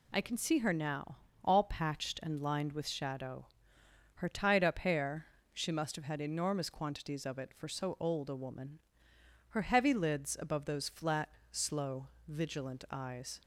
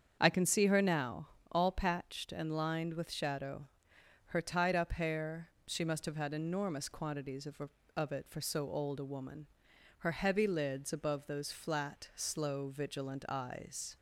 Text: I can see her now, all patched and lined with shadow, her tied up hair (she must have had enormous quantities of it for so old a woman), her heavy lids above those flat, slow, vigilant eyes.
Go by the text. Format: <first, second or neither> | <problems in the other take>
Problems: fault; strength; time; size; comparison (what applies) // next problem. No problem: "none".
first | starts louder than the rest; strong; until 1.2 s; 7.5 dB // says "of" twice; at 7.9 s